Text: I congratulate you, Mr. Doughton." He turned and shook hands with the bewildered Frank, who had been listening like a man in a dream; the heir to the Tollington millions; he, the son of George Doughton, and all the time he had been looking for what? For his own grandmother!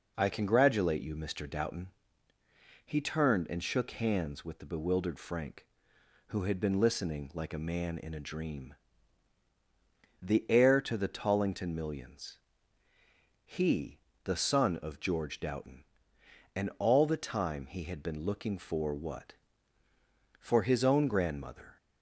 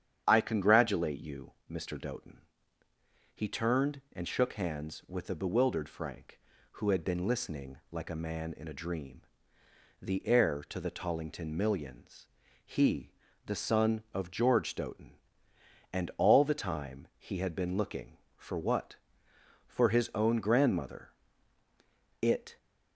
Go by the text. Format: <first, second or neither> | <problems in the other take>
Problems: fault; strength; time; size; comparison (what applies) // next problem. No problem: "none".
first | starts louder than the rest; strong; until 1.2 s; 9 dB // goes on to say "It"; slight; from 22.2 s on; 0.36 s long